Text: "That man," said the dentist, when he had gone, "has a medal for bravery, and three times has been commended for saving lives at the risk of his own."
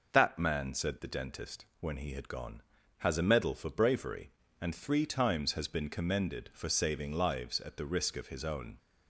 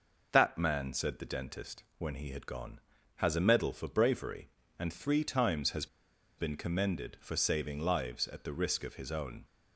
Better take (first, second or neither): first